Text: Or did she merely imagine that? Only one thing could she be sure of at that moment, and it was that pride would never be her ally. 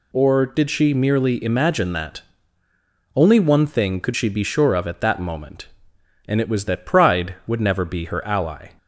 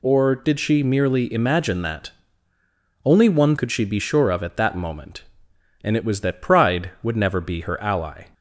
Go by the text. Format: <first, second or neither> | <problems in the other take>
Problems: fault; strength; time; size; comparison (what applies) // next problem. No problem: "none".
first | skips "thing"; at 3.5 s